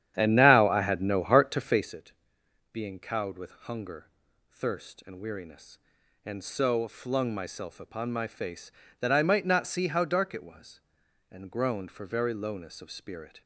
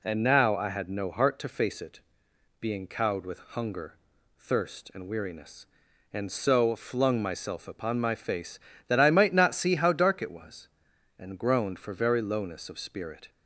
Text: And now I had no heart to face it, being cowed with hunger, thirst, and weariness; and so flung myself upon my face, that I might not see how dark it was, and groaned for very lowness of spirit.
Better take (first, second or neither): second